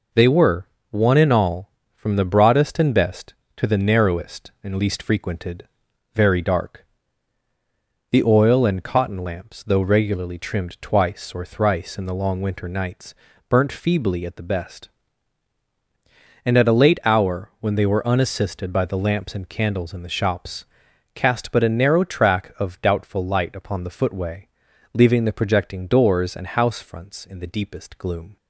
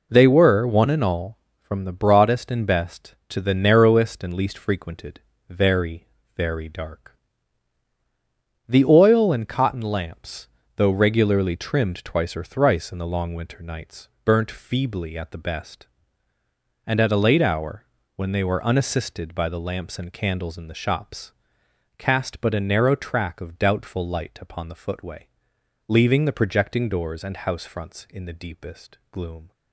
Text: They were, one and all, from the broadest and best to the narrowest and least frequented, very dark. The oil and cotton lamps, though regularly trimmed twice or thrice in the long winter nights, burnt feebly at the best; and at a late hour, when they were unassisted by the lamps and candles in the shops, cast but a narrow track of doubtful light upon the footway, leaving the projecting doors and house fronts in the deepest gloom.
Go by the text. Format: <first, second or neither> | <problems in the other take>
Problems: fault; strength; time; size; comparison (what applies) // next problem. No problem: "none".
first | says "very" twice; at 6.3 s